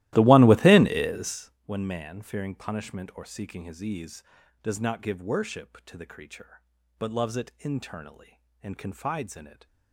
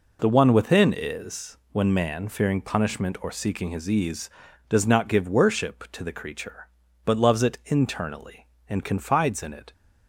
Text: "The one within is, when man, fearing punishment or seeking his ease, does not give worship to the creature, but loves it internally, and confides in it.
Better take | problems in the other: second | starts louder than the rest; strong; until 1.6 s; 16 dB

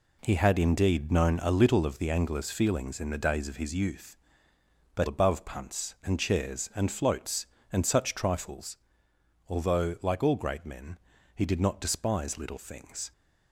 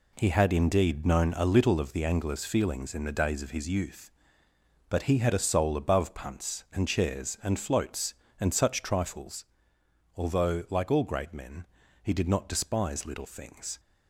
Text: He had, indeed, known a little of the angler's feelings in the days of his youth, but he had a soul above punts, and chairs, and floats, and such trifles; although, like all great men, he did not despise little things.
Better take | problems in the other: second | skips "he had a soul"; at 5.0 s

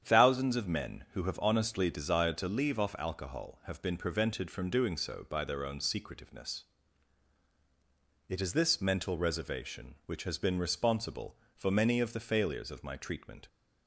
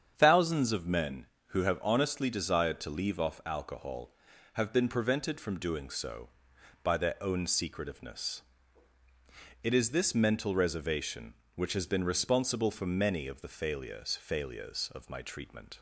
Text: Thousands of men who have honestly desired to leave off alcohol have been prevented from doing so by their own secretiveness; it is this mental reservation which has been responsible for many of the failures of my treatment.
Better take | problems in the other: first | starts louder than the rest; strong; until 1.1 s; 8 dB; strong in the first // says "failures" twice; at 14.1 s

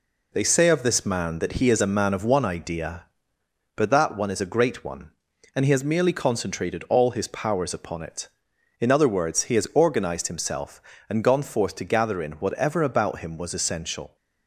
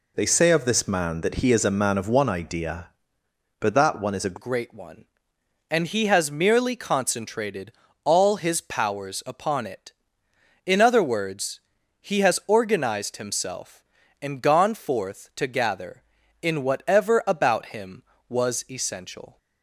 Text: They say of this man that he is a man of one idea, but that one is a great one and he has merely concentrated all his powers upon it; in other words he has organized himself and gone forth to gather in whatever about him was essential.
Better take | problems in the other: first | changes voice at "great"; from 4.3 s on; 15.0 s long // pauses between "concentrated" and "all"; slight; at 7.7 s; 0.32 s long // pauses between "words" and "he"; at 11.5 s; 0.40 s long

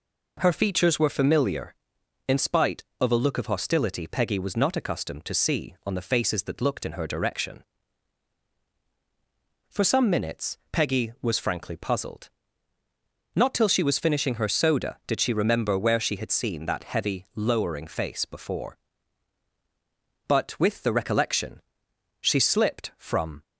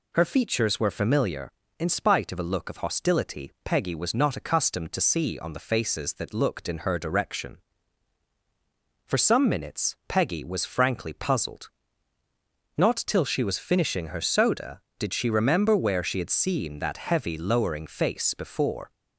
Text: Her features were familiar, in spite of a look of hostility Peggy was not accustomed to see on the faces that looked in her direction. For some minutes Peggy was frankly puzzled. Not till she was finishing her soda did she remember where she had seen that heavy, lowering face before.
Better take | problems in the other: second | goes on to say "But with the recollection she slipped from"; strong; from 20.2 s on; 3.1 s long

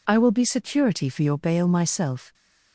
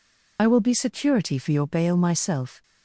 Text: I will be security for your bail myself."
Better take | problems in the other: first | loses the start of "I"; at 0.3 s; 35 ms

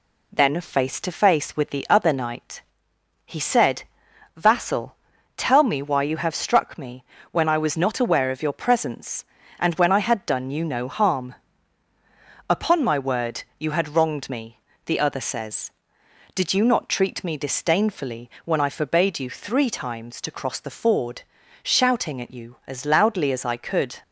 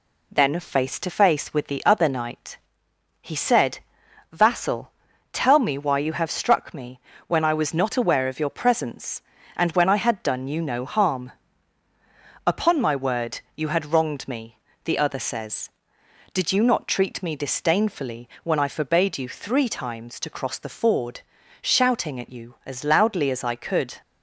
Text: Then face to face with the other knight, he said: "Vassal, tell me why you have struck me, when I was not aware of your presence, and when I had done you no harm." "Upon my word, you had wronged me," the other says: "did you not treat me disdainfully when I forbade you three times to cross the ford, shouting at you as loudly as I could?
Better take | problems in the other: neither | none

